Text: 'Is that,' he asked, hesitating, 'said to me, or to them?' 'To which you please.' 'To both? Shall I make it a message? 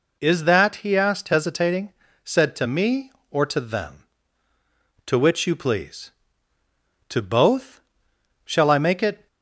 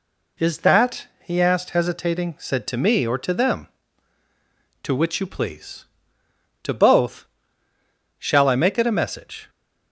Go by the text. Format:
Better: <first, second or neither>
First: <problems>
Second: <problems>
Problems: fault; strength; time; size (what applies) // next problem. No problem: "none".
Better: second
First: stops before "a message"; at 9.2 s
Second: none